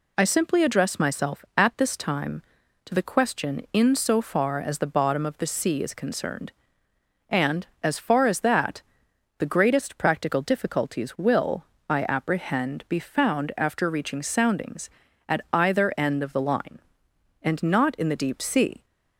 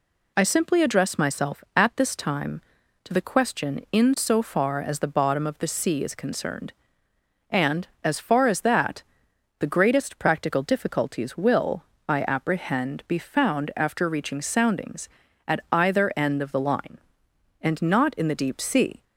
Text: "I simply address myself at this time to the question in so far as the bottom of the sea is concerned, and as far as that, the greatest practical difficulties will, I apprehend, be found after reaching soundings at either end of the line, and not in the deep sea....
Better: neither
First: none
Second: none

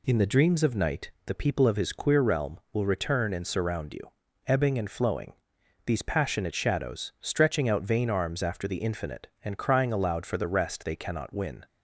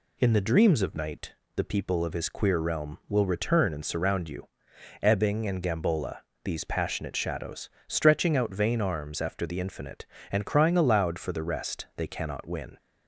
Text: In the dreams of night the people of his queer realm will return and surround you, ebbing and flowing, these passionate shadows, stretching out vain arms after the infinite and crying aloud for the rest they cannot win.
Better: first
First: pauses between "night" and "the"; slight; at 1.0 s; 0.16 s long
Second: pauses between "night" and "the"; slight; at 1.3 s; 0.22 s long // says "gambola" for "flowing"; at 5.6 s

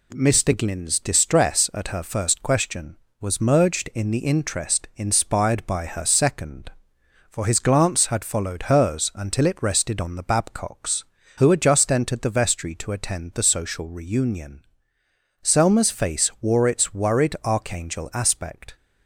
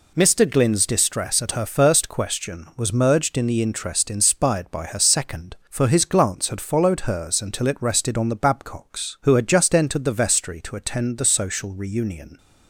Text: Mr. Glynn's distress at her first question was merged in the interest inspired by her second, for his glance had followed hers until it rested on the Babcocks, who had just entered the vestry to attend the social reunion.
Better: second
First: goes on to say "Selma's face wore its worried archangel aspect"; strong; from 15.4 s on; 3.3 s long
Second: none

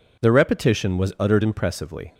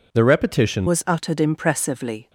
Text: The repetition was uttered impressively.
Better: first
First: none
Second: changes voice at "was"; from 0.8 s on; 1.4 s long

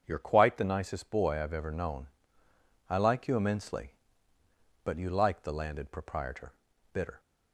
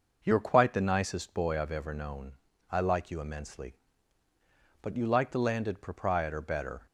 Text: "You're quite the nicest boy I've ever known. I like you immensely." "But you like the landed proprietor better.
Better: second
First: starts louder than the rest; strong; until 1.0 s; 7 dB // says "bitter" for "better"; at 6.9 s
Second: none

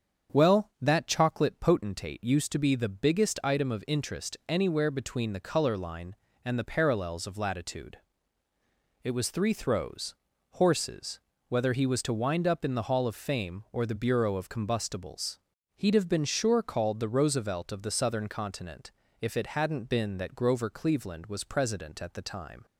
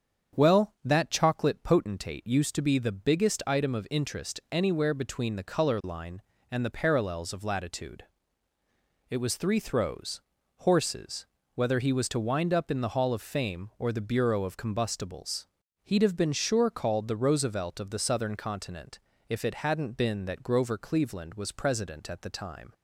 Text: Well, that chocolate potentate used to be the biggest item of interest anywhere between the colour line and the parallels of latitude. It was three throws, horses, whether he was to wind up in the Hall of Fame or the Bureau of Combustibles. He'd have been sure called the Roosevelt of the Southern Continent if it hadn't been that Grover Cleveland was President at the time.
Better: neither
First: starts louder than the rest; strong; until 1.4 s; 7.5 dB // pauses between "Continent" and "if"; slight; at 18.9 s; 0.30 s long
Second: starts louder than the rest; strong; until 1.4 s; 7.5 dB // pauses between "Continent" and "if"; slight; at 18.9 s; 0.30 s long

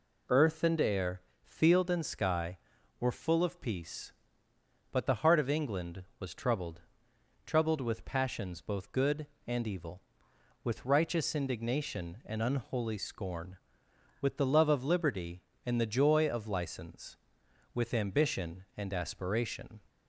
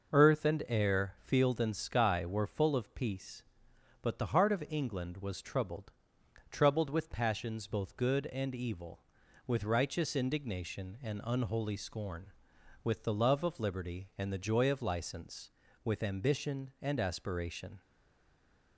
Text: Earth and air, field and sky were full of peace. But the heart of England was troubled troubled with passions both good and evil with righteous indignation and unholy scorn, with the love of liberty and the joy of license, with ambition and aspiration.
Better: first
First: pauses between "troubled" and "troubled"; noticeable; at 6.8 s; 0.64 s long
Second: pauses between "troubled" and "troubled"; noticeable; at 5.9 s; 0.58 s long // stays silent after the last word; slight; from 17.8 s on; 0.9 s long

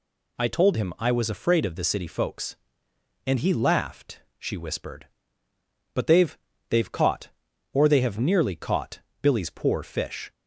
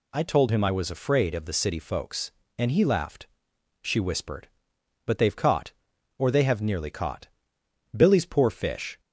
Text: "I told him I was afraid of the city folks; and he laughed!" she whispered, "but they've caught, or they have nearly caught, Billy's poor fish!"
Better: second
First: says "they've" twice; at 6.6 s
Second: none

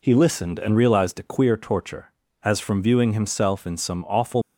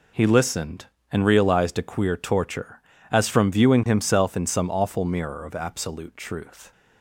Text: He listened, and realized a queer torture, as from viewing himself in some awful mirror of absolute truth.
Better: second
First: stops before "mirror of absolute truth"; at 4.4 s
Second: none

